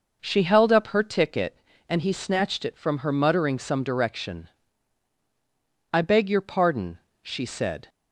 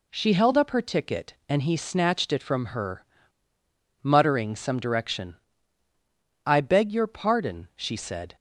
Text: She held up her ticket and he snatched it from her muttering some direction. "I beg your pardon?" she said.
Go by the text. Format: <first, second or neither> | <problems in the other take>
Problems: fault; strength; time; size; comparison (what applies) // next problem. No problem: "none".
first | pauses between "her" and "muttering"; noticeable; at 3.0 s; 0.97 s long